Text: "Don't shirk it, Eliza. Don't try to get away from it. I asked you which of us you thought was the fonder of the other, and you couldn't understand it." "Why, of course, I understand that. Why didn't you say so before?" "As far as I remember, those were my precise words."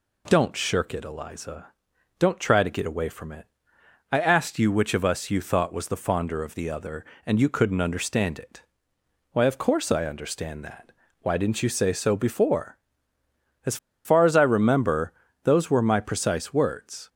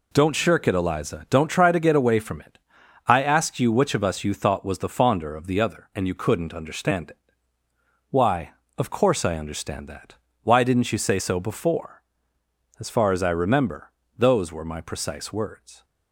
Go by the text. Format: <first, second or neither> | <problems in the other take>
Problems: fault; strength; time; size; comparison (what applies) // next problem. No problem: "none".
second | pauses between "As" and "far"; slight; at 13.7 s; 0.28 s long